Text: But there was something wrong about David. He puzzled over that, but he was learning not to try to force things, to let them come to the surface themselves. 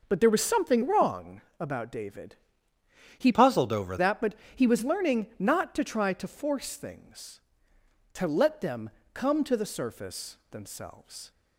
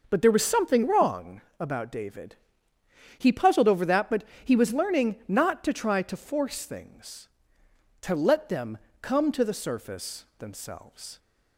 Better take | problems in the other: second | pauses between "wrong" and "about"; slight; at 1.4 s; 0.18 s long; slight in the second // changes voice from "puzzled" to "over"; from 3.3 to 3.9 s; 0.6 s long // pauses between "but" and "he"; slight; at 4.3 s; 0.20 s long; slight in the second // pauses between "them" and "come"; slight; at 8.9 s; 0.22 s long; slight in the second

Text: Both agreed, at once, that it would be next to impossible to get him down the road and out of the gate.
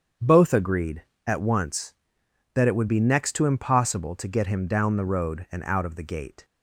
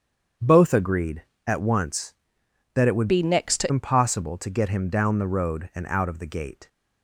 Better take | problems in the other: first | starts louder than the rest; strong; until 1.6 s; 7.5 dB; strong in the first // changes voice from "be" to "to"; from 3.0 to 3.7 s; 0.7 s long

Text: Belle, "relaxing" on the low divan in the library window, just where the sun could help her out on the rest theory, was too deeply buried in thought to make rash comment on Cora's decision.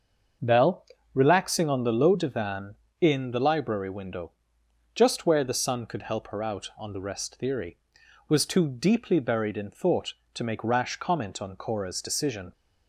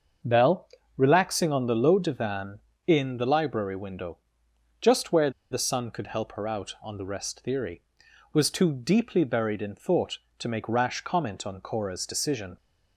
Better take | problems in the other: first | starts louder than the rest; until 1.5 s; 6.5 dB; also in the first // pauses between "where" and "the"; slight; at 5.2 s; 0.21 s long

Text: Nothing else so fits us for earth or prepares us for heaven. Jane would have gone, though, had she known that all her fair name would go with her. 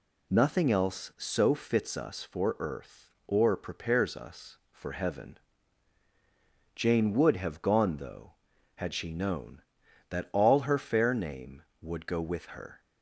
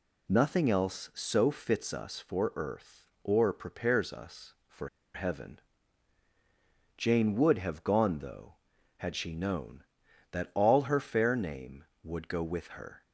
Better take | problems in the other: first | pauses between "for" and "heaven"; slight; at 4.8 s; 0.25 s long

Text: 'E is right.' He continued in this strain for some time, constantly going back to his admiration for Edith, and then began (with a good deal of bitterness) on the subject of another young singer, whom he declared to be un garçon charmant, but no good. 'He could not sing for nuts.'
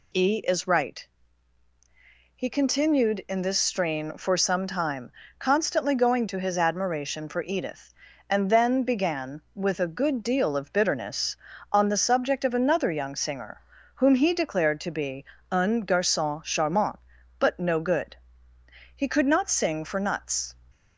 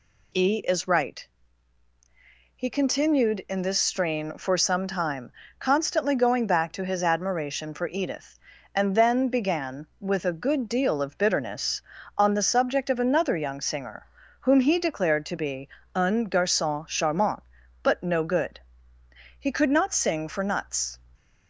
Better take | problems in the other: second | skips "back"; at 6.2 s // pauses between "be" and "un"; slight; at 15.2 s; 0.26 s long; slight in the second

